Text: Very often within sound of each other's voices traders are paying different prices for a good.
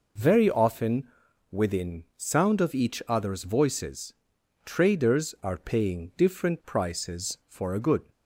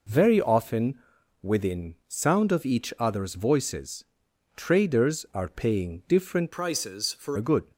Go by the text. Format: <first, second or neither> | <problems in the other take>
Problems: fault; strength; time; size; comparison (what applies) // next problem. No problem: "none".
first | pauses between "often" and "within"; noticeable; at 0.9 s; 0.46 s long; noticeable in the first // pauses between "voices" and "traders"; noticeable; at 4.0 s; 0.50 s long; noticeable in the first // changes voice from "prices" to "for"; from 6.5 to 7.3 s; 0.8 s long